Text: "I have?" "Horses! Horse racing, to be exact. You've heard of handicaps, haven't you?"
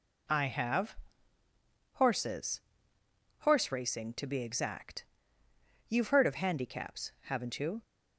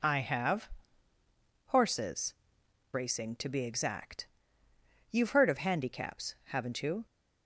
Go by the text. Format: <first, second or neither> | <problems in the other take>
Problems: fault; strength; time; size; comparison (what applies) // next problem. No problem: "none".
first | skips "Horse"; at 2.6 s